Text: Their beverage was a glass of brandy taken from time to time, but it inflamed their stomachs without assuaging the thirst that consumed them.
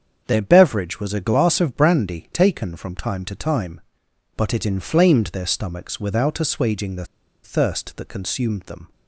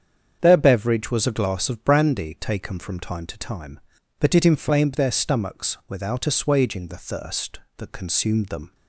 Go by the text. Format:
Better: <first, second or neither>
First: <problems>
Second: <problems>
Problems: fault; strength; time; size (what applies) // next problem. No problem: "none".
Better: second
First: starts louder than the rest; strong; until 1.2 s; 7.5 dB // pauses between "the" and "thirst"; at 7.0 s; 0.39 s long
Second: starts louder than the rest; strong; until 1.4 s; 7.5 dB